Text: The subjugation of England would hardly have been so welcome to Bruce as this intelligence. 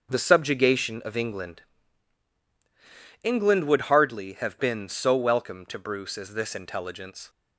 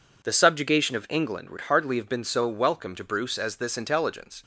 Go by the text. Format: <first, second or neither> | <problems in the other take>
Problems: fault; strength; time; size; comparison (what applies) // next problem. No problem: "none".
second | starts louder than the rest; until 1.1 s; 6.5 dB // says "England" twice; at 3.2 s